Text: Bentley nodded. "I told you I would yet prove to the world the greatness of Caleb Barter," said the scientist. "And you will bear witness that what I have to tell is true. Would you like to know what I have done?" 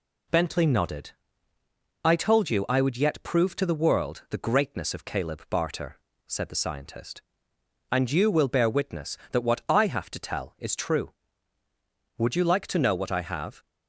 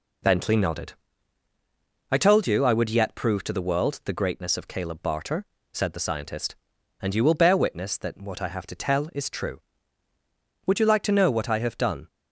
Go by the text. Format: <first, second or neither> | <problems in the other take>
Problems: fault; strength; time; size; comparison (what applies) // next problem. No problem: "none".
second | stops before "done"; at 13.6 s